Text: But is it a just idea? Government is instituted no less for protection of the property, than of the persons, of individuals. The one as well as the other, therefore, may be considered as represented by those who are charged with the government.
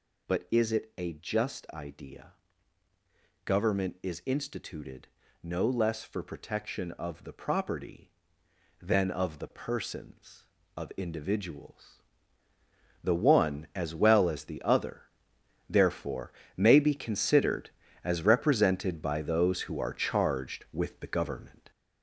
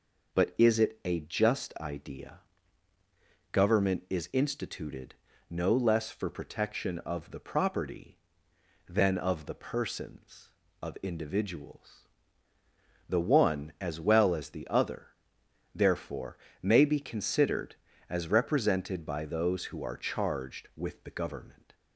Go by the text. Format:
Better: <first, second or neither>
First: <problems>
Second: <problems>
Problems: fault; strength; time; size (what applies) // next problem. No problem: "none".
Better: second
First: gets louder; noticeable; throughout; 6 dB // pauses between "instituted" and "no"; slight; at 5.0 s; 0.36 s long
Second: pauses between "instituted" and "no"; slight; at 5.1 s; 0.36 s long